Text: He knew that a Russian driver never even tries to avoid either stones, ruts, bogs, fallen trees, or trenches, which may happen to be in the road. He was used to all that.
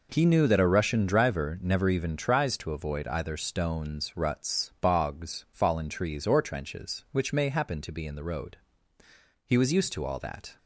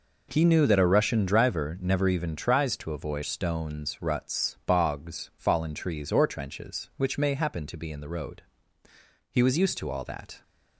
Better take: first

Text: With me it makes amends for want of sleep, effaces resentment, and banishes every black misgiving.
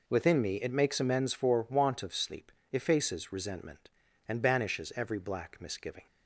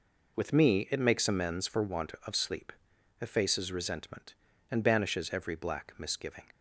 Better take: second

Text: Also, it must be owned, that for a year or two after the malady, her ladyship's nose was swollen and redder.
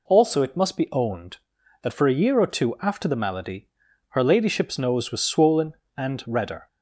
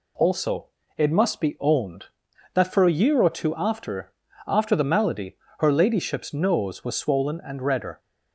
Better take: first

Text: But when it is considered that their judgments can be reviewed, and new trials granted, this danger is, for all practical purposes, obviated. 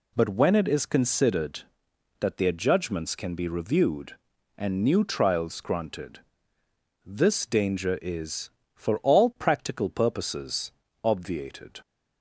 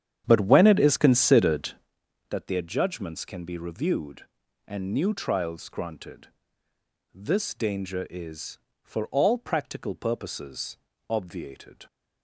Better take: first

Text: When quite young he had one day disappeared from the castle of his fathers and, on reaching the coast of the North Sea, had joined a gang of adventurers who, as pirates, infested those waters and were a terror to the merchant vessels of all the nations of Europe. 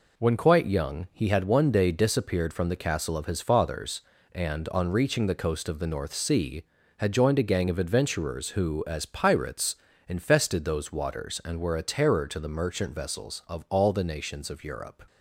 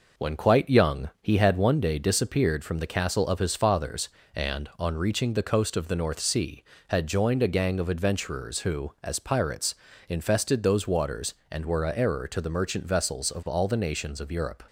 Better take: first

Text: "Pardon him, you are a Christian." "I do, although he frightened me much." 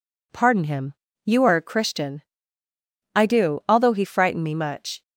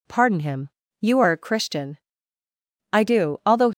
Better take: first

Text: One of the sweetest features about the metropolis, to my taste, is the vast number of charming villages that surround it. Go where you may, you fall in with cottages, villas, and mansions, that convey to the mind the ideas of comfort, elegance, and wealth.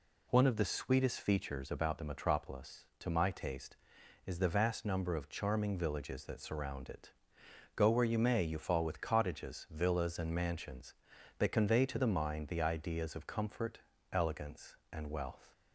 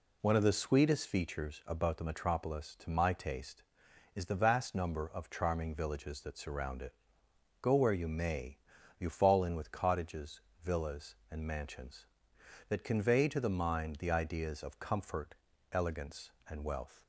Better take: second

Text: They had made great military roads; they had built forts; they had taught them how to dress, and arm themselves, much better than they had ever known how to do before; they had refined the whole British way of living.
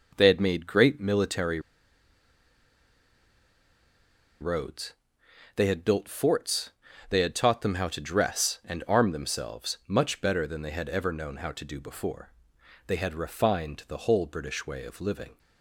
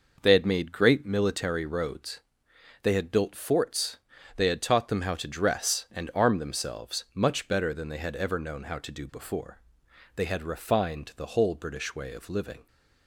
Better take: second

